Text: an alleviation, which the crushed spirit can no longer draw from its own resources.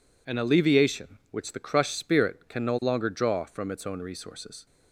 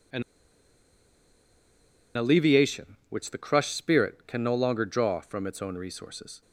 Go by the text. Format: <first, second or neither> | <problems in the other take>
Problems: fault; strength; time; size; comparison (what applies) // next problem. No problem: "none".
first | pauses between "an" and "alleviation"; strong; at 0.2 s; 1.9 s long